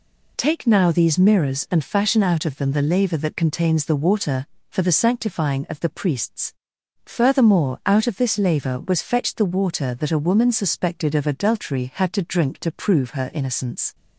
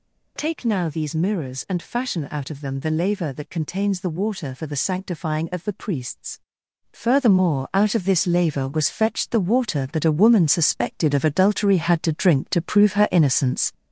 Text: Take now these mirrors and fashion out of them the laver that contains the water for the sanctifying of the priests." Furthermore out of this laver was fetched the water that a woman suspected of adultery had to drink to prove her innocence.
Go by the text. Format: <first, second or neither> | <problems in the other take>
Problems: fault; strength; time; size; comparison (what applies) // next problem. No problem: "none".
first | gets louder; noticeable; throughout; 4 dB